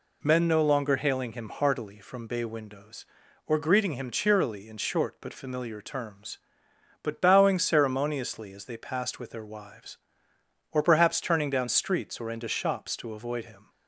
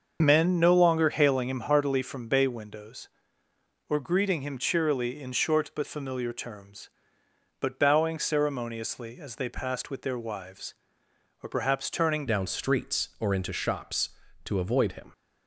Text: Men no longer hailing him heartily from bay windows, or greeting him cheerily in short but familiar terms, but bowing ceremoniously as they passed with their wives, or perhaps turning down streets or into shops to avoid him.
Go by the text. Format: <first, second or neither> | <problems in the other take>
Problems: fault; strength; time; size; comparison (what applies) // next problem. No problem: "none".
first | starts louder than the rest; until 1.2 s; 6.5 dB // changes voice at "down"; from 12.2 s on; 2.9 s long